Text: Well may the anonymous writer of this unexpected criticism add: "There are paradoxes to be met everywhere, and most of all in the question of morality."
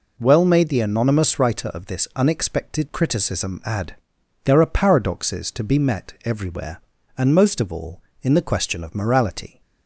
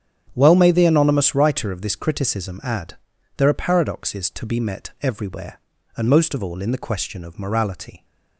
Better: first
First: none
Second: starts louder than the rest; strong; until 1.3 s; 9 dB // skips "unexpected"; at 1.9 s

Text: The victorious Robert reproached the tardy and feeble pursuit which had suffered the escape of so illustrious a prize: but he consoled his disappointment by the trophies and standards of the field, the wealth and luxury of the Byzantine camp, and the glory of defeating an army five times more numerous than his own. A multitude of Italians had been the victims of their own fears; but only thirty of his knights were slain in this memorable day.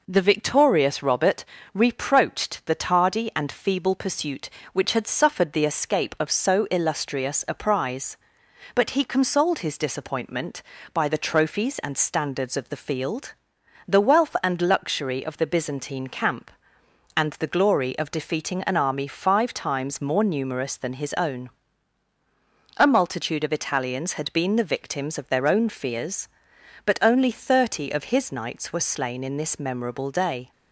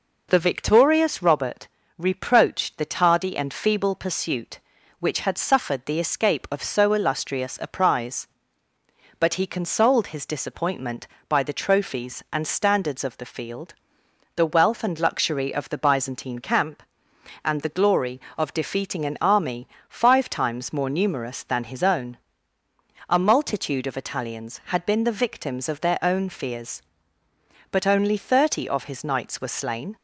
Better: first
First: pauses between "Robert" and "reproached"; slight; at 1.4 s; 0.28 s long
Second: pauses between "Robert" and "reproached"; slight; at 1.6 s; 0.30 s long // pauses between "army" and "five"; slight; at 19.6 s; 0.20 s long // stops before "in this memorable day"; at 29.9 s

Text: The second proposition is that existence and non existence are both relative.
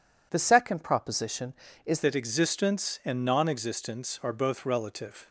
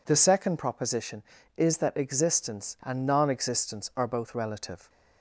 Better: second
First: changes voice at "that"; from 2.0 s on; 3.2 s long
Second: none

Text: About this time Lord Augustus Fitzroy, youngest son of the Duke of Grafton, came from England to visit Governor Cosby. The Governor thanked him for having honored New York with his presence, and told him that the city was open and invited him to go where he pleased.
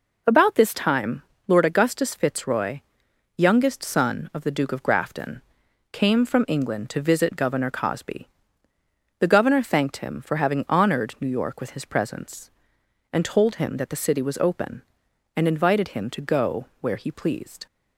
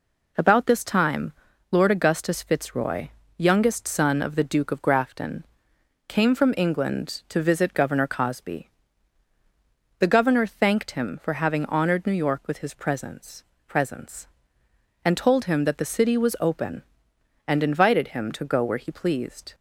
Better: first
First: pauses between "time" and "Lord"; slight; at 1.2 s; 0.26 s long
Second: pauses between "time" and "Lord"; at 1.3 s; 0.40 s long // says "presence" twice; at 13.6 s

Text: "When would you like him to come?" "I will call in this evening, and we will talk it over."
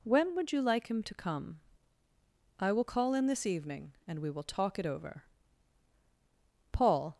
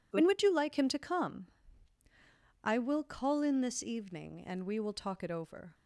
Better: second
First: goes on to say "Paul"; slight; from 6.7 s on; 0.46 s long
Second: none

